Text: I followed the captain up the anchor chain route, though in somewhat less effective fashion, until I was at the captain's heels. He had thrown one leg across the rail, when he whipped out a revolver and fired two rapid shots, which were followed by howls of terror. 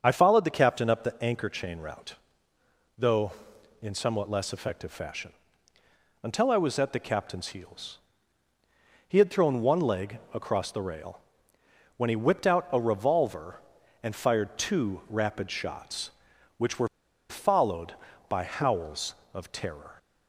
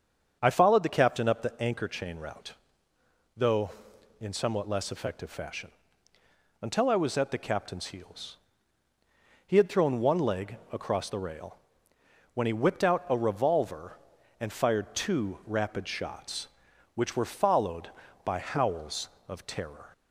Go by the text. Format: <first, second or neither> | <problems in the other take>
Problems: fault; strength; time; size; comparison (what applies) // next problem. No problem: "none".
second | starts louder than the rest; until 1.0 s; 7 dB; also in the second // pauses between "were" and "followed"; at 16.8 s; 0.41 s long